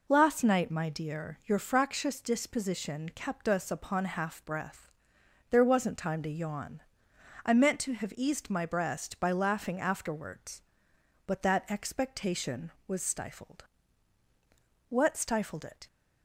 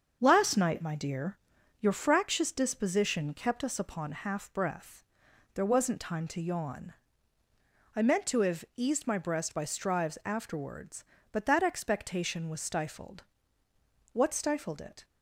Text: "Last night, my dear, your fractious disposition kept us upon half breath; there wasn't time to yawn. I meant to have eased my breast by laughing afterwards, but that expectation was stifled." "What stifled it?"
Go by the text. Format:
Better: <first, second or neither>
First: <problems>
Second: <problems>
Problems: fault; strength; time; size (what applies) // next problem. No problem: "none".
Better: first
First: none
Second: starts louder than the rest; until 1.2 s; 7 dB // says "strives" for "laughing"; at 9.6 s